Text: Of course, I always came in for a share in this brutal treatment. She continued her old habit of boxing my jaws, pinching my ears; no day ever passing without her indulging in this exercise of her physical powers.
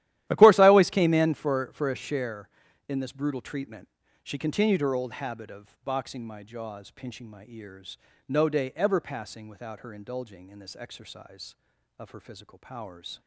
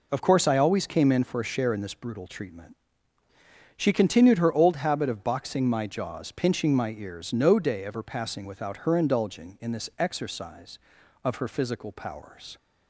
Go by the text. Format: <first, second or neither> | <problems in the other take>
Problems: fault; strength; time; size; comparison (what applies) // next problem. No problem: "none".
second | starts louder than the rest; strong; until 1.2 s; 13.5 dB // says "for" twice; at 1.7 s